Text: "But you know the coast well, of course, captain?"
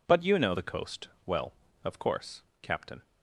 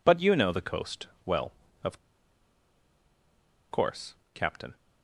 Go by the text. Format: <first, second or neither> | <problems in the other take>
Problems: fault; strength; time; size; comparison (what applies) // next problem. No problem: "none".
first | pauses between "coast" and "well"; slight; at 1.0 s; 0.18 s long; slight in the first // pauses between "of" and "course"; strong; at 1.9 s; 1.7 s long